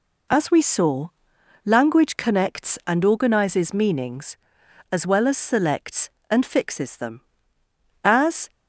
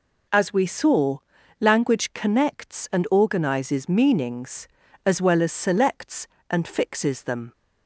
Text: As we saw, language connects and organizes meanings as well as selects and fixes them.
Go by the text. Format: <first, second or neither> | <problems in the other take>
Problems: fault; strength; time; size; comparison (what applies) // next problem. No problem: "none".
second | goes on to say "As"; slight; from 8.0 s on; 0.46 s long